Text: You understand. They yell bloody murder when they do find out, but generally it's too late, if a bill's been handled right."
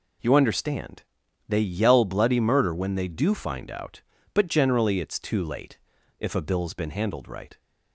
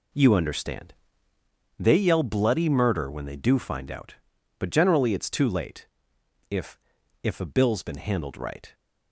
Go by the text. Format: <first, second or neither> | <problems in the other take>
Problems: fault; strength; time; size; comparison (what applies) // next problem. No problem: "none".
first | says "if" twice; at 7.2 s